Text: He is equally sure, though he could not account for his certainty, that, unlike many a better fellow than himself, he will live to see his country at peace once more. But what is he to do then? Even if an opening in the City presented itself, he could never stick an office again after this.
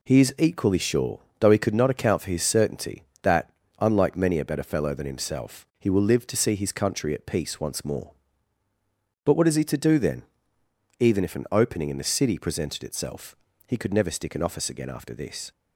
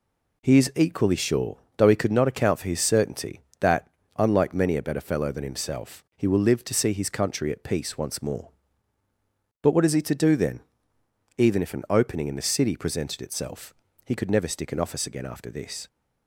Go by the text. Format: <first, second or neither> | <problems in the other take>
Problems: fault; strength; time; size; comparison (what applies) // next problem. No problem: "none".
neither | none